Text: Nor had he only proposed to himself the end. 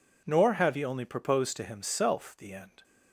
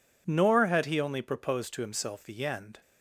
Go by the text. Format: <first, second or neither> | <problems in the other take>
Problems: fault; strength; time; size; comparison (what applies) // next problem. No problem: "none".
second | says "have" for "had"; at 0.5 s